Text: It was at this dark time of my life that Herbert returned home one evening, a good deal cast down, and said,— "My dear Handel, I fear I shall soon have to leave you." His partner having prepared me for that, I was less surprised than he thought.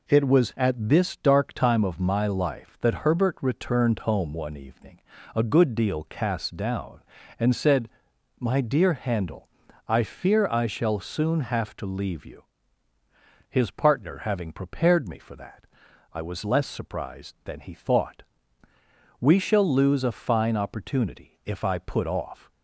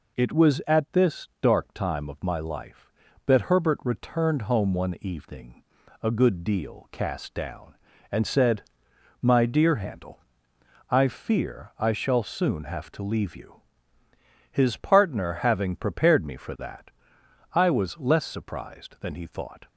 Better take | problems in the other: second | goes on to say "We shall lose a fine opportunity if I put off"; strong; from 19.1 s on; 3.3 s long

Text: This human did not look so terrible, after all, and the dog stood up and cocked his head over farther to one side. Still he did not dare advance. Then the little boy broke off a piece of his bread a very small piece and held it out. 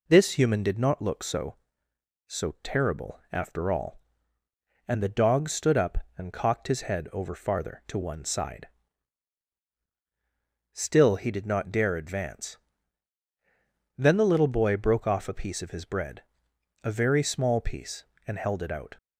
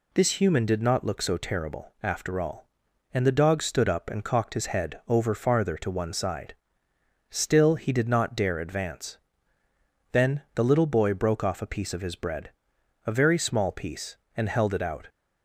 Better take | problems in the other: second | says "so" twice; at 2.2 s // pauses between "bread" and "a"; noticeable; at 16.2 s; 0.60 s long; noticeable in the second

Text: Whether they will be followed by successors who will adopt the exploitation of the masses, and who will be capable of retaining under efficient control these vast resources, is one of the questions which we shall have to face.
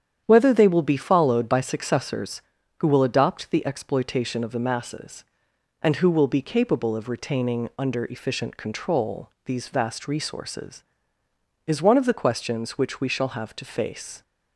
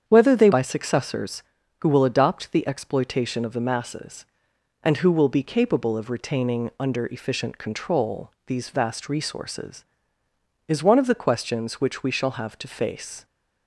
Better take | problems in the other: first | starts louder than the rest; strong; until 1.0 s; 8 dB; strong in the first // skips "will be followed"; at 0.5 s

